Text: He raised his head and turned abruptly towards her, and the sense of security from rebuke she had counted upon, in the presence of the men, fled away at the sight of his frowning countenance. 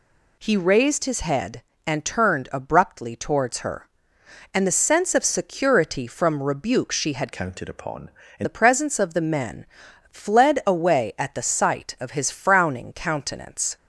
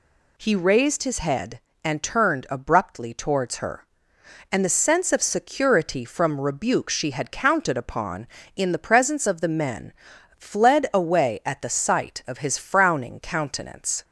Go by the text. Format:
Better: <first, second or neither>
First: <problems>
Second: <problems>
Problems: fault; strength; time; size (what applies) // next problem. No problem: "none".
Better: second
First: changes voice from "counted" to "in"; from 7.3 to 8.4 s; 1.1 s long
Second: none